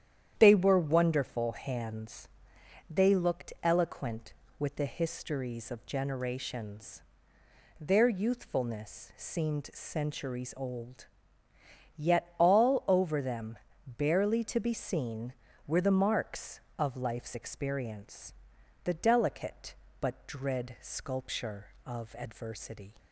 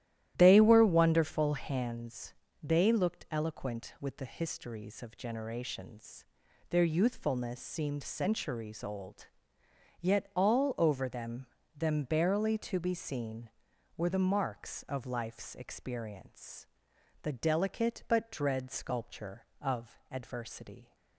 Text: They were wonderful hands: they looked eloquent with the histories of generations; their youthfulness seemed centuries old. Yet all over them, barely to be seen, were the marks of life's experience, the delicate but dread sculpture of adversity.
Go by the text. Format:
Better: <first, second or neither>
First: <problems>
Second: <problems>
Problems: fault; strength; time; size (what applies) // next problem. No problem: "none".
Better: first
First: starts louder than the rest; strong; until 1.4 s; 10 dB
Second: starts louder than the rest; strong; until 1.3 s; 13 dB // says "them" twice; at 11.7 s